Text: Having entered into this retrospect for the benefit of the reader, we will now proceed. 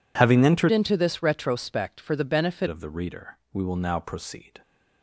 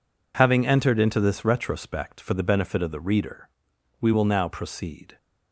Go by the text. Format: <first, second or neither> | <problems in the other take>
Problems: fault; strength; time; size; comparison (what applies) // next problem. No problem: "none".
second | changes voice from "into" to "benefit"; from 0.6 to 2.6 s; 2.0 s long